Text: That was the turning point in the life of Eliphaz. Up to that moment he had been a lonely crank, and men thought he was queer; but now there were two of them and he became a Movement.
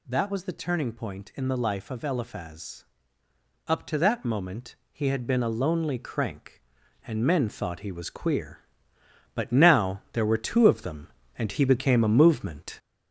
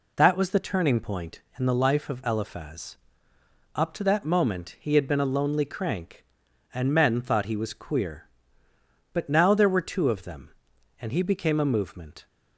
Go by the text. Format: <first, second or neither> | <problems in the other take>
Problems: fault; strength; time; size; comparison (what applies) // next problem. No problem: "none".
second | gets louder; noticeable; throughout; 4.5 dB // pauses between "moment" and "he"; slight; at 4.7 s; 0.16 s long